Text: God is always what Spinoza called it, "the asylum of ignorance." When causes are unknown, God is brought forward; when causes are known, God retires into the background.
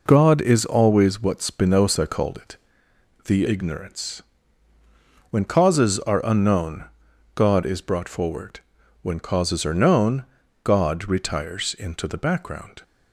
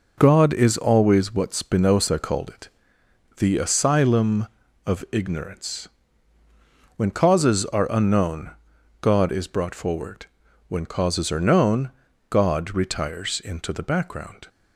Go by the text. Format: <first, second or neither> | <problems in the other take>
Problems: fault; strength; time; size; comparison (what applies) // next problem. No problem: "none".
second | skips "asylum of"; at 3.4 s